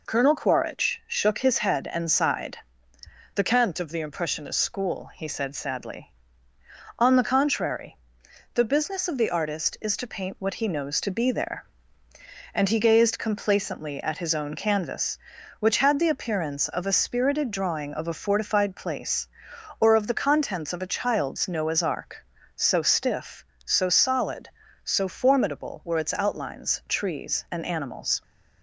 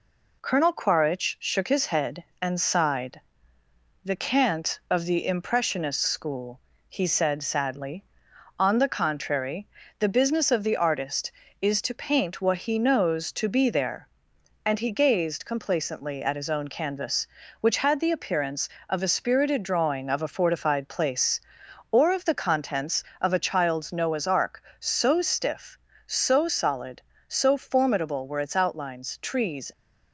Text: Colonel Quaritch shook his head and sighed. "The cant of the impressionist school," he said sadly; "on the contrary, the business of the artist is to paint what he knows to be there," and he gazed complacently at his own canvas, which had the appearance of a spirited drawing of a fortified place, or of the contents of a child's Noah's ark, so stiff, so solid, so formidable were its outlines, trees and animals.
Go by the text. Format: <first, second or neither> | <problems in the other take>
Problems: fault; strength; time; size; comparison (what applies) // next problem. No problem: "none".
first | stops before "and animals"; at 29.7 s